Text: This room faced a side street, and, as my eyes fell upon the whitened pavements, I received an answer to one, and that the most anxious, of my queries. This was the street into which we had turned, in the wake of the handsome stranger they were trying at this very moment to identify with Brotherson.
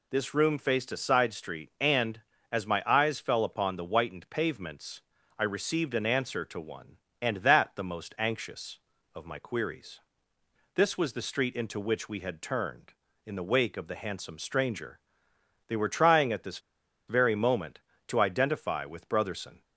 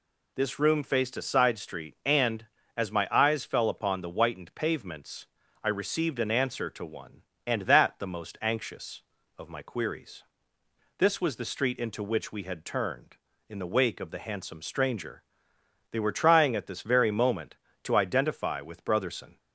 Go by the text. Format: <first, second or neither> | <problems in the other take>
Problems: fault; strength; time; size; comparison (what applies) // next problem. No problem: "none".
second | pauses between "stranger" and "they"; noticeable; at 15.0 s; 0.68 s long; noticeable in the second // pauses between "this" and "very"; noticeable; at 16.5 s; 0.49 s long